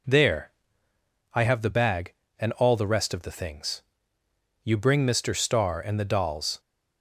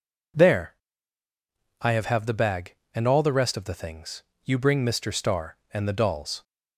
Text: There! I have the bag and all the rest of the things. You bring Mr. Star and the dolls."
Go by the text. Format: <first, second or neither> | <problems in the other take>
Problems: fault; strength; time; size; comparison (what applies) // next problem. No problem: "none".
first | says "have" twice; at 2.0 s